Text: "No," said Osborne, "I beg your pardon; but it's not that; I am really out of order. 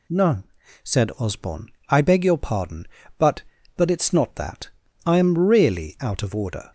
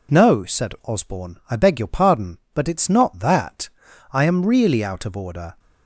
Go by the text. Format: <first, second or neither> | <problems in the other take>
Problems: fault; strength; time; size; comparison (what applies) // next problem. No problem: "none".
second | says "but" twice; at 3.7 s